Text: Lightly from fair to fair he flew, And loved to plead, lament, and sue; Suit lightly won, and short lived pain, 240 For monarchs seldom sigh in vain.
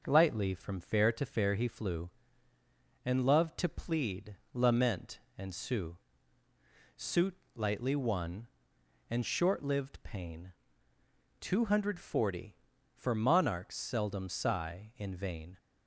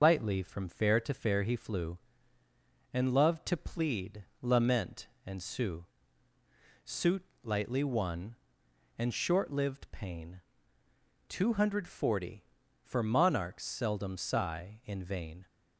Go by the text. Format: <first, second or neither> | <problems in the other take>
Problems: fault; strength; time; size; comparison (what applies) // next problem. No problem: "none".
first | loses the start of "Lightly"; at 0.0 s; 95 ms // pauses between "Suit" and "lightly"; slight; at 7.2 s; 0.18 s long; slight in the first